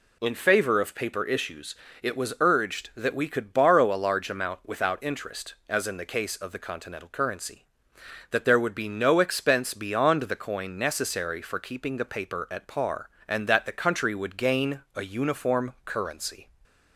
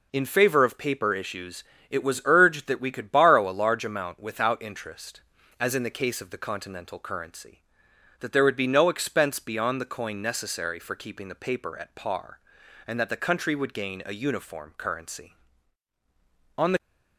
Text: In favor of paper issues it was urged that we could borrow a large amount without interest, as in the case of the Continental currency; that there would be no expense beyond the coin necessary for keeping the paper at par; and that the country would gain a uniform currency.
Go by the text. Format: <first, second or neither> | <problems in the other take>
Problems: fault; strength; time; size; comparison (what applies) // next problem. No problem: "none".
first | pauses between "issues" and "it"; slight; at 1.6 s; 0.26 s long; slight in the first // goes on to say "On the"; slight; from 16.5 s on; 0.22 s long